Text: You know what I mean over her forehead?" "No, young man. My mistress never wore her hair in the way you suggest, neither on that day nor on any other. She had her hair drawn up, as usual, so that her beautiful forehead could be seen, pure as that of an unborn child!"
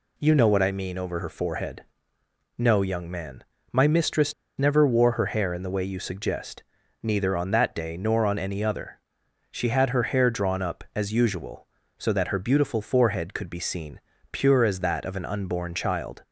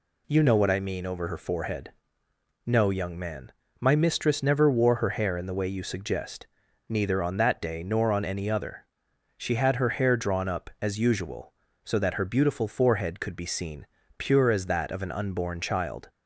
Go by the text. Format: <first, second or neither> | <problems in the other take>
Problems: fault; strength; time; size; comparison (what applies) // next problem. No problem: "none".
second | pauses between "mistress" and "never"; slight; at 4.3 s; 0.25 s long